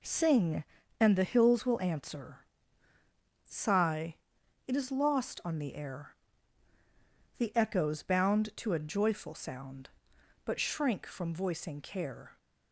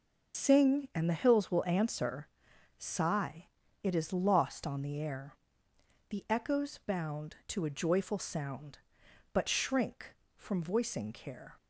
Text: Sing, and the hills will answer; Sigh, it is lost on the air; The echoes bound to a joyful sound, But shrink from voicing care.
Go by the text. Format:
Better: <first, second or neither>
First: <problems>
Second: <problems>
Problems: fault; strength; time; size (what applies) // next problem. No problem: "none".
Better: first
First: none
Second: loses the start of "Sing"; at 0.3 s; 120 ms